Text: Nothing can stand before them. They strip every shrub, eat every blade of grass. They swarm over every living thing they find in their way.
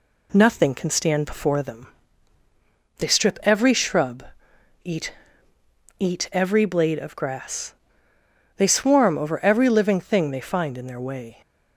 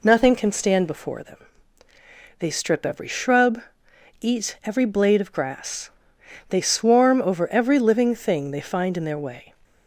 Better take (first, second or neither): second